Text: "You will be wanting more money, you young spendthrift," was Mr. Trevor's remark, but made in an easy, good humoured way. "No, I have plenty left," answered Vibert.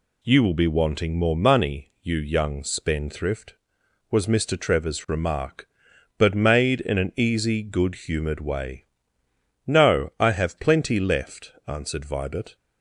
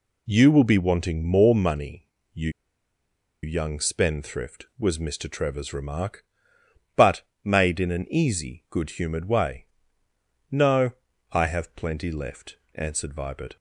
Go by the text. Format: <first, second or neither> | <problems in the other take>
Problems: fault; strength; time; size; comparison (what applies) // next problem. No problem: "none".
first | pauses between "you" and "young"; noticeable; at 2.4 s; 0.94 s long // pauses between "but" and "made"; slight; at 7.2 s; 0.20 s long